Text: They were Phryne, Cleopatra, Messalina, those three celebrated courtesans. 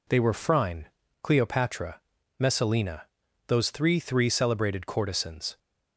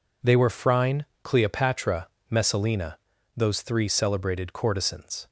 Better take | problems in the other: second | says "three" twice; at 4.0 s

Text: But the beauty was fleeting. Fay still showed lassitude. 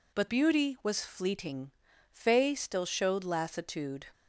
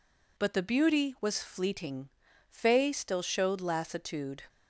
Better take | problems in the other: second | skips "the"; at 0.2 s

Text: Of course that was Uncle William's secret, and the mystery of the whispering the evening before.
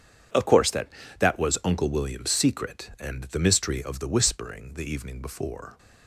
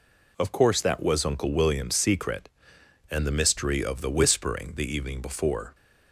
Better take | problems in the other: second | says "that" twice; at 1.1 s

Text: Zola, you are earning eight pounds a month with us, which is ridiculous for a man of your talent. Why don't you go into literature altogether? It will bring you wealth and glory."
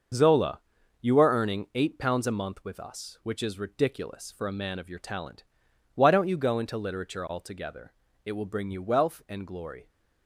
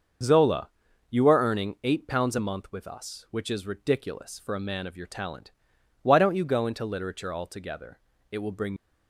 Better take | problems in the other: first | starts louder than the rest; until 1.6 s; 6.5 dB; also in the first // stops before "you wealth and glory"; at 8.7 s

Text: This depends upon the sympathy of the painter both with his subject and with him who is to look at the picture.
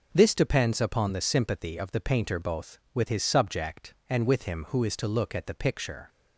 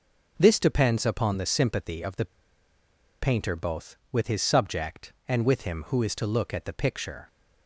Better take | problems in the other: first | pauses between "the" and "painter"; noticeable; at 2.2 s; 0.94 s long

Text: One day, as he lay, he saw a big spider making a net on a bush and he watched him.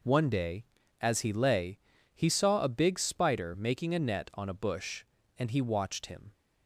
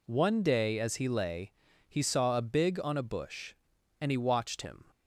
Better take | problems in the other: first | skips "spider making a net"; at 2.8 s

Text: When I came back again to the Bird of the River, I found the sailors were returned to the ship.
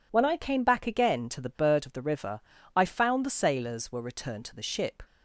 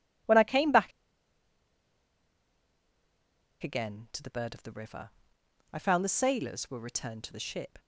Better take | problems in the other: first | pauses between "back" and "again"; strong; at 0.9 s; 2.7 s long

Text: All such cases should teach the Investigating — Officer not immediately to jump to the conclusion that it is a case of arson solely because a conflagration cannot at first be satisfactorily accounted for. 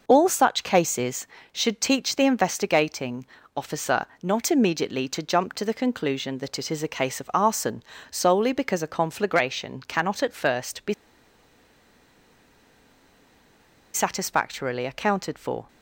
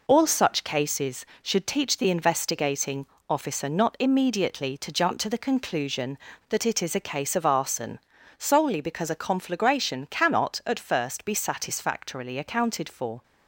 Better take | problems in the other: second | pauses between "Officer" and "not"; slight; at 4.0 s; 0.16 s long // pauses between "arson" and "solely"; slight; at 7.8 s; 0.30 s long; also in the second // pauses between "be" and "satisfactorily"; strong; at 10.9 s; 3.0 s long

